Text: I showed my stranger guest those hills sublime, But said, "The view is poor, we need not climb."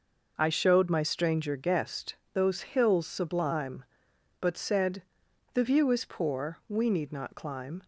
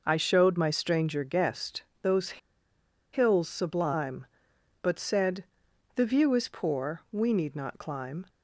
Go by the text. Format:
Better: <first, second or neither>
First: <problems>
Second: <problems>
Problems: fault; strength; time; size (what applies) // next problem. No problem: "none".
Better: first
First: pauses between "guest" and "those"; slight; at 2.1 s; 0.17 s long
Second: pauses between "guest" and "those"; slight; at 1.8 s; 0.18 s long // pauses between "those" and "hills"; noticeable; at 2.3 s; 0.74 s long